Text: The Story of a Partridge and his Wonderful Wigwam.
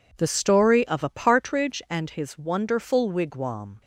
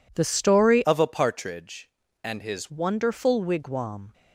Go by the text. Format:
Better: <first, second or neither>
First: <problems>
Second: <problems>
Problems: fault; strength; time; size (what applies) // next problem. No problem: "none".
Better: first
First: none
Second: changes voice from "of" to "his"; from 0.8 to 2.7 s; 1.9 s long